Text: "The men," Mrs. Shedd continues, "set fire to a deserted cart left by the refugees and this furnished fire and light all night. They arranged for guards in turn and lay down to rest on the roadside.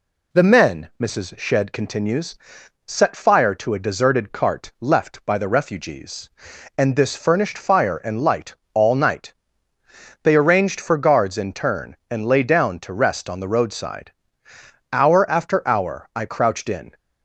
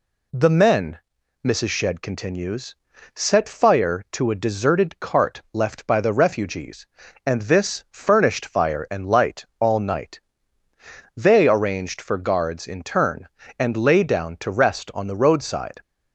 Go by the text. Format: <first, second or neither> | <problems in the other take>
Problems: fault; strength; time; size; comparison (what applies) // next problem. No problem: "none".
second | pauses between "light" and "all"; slight; at 8.5 s; 0.18 s long // goes on to say "Hour after hour I crouched in"; strong; from 14.9 s on; 2.0 s long